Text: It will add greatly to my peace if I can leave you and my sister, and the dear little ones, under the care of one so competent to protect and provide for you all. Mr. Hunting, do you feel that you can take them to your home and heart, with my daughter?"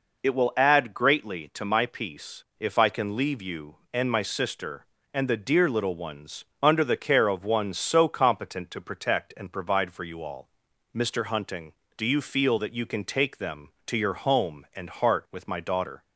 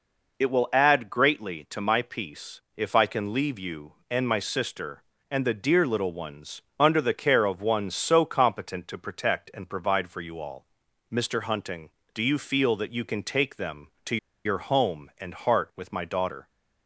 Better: first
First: none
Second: pauses between "to" and "your"; slight; at 14.1 s; 0.28 s long

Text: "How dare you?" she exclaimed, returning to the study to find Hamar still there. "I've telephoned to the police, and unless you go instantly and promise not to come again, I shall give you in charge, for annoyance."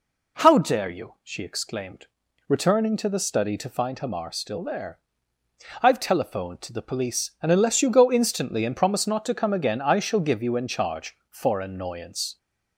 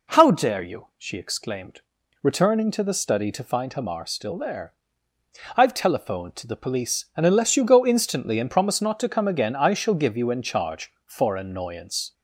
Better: neither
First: none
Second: none

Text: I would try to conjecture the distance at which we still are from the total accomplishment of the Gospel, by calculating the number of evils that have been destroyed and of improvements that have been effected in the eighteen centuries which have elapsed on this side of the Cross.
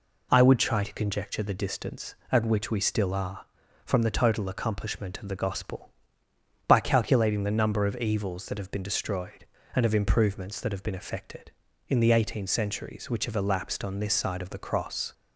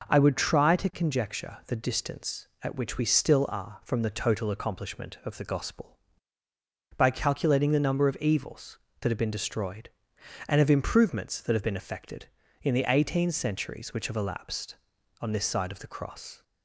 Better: neither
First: none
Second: none

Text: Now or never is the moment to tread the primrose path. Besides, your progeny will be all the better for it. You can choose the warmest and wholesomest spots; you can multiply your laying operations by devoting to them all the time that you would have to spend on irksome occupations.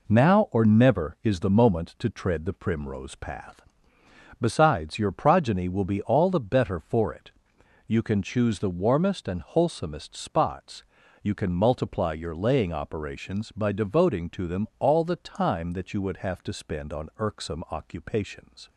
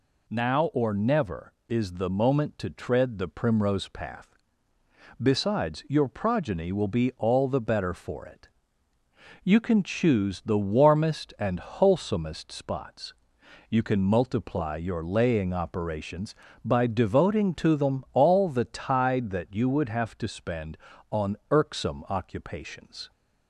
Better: first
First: none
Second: says "tide" for "time"; at 18.6 s

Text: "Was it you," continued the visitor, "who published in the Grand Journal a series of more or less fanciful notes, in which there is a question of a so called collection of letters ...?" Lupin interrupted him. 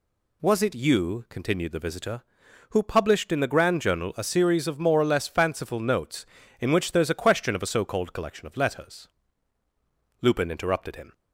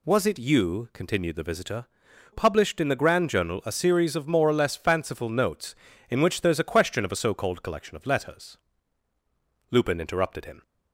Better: first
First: none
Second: skips "who"; at 2.0 s

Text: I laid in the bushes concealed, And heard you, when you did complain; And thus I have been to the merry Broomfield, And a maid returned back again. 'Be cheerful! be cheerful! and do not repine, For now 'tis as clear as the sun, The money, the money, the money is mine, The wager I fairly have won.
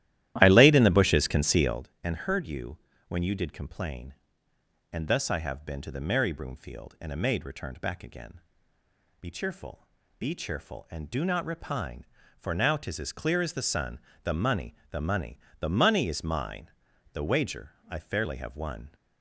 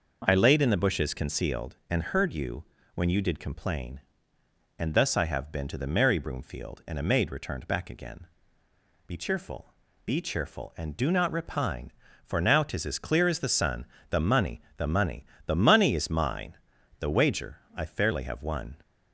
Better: second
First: starts louder than the rest; strong; until 1.9 s; 13.5 dB // pauses between "wager" and "I"; slight; at 17.7 s; 0.18 s long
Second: pauses between "wager" and "I"; slight; at 17.5 s; 0.18 s long

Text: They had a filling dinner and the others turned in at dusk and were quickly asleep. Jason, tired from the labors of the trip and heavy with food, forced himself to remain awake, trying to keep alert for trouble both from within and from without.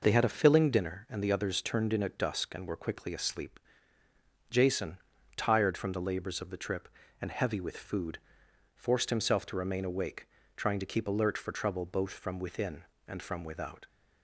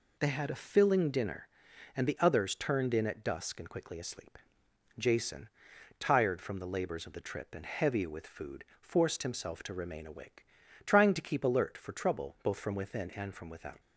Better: first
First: none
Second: skips "were"; at 3.6 s

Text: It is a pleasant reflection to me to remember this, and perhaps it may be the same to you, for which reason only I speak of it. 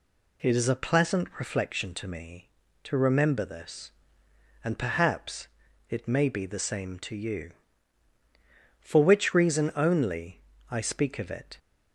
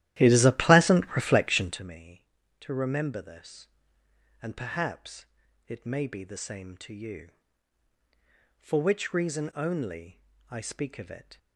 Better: first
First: pauses between "perhaps" and "it"; at 5.4 s; 0.42 s long // pauses between "only" and "I"; slight; at 10.3 s; 0.30 s long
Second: starts louder than the rest; strong; until 1.9 s; 13.5 dB // pauses between "perhaps" and "it"; at 5.2 s; 0.42 s long // pauses between "only" and "I"; slight; at 10.1 s; 0.30 s long

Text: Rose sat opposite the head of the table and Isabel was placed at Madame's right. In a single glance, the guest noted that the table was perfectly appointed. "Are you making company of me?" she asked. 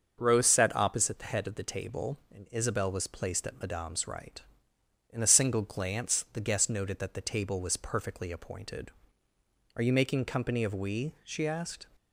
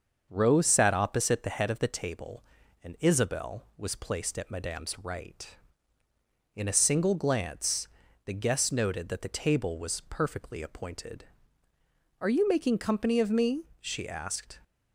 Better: second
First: starts louder than the rest; until 1.2 s; 6.5 dB // says "we" for "me"; at 10.7 s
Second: starts louder than the rest; until 1.3 s; 6.5 dB

